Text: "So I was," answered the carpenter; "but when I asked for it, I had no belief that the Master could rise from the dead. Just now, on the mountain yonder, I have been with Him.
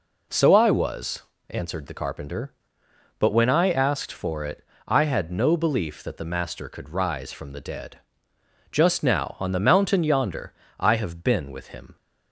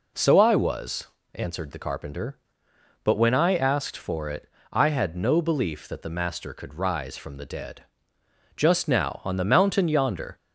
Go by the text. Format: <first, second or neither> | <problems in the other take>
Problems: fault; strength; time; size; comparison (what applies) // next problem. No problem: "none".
first | stops before "I have been with Him"; at 10.3 s